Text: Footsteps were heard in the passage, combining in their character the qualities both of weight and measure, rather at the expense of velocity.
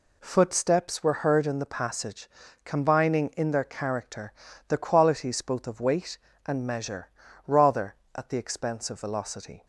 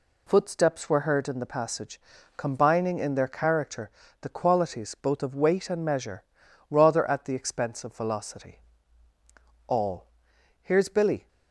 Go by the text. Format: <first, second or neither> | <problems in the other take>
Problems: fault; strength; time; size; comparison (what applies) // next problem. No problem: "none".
first | pauses between "character" and "the"; slight; at 3.8 s; 0.30 s long; slight in the first // goes on to say "All Here's Billy"; from 9.6 s on; 1.6 s long